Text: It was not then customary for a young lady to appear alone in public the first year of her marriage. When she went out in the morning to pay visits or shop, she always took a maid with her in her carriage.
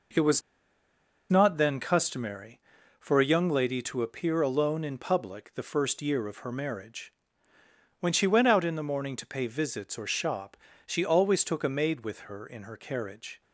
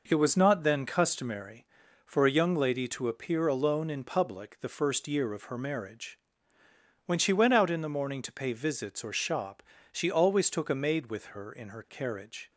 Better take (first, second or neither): second